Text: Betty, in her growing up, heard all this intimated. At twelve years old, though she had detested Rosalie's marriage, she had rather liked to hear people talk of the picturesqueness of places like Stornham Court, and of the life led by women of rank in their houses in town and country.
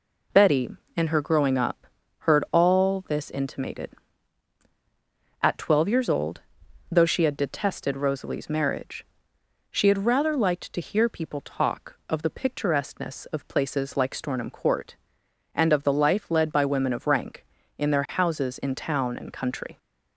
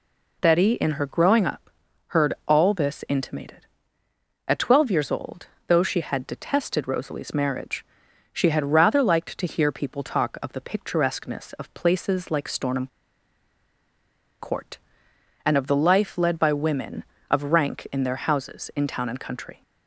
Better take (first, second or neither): first